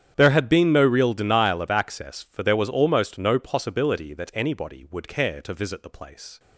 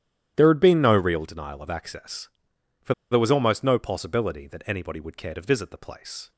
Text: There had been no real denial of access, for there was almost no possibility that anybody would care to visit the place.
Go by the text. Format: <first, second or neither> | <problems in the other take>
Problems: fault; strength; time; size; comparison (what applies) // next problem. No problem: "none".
first | starts louder than the rest; strong; until 1.3 s; 11 dB; strong in the first // pauses between "for" and "there"; slight; at 2.9 s; 0.17 s long